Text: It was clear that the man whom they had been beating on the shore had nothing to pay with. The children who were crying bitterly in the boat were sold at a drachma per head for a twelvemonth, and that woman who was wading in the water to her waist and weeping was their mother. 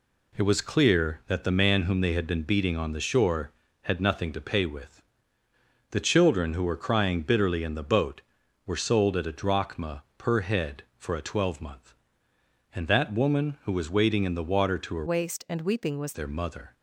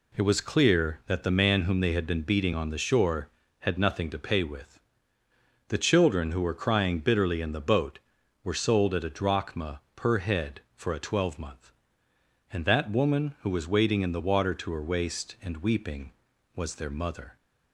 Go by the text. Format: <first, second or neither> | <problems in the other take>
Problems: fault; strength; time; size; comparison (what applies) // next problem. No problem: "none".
second | pauses between "drachma" and "per"; slight; at 10.0 s; 0.16 s long; slight in the second // changes voice from "waist" to "was"; from 15.0 to 16.1 s; 1.1 s long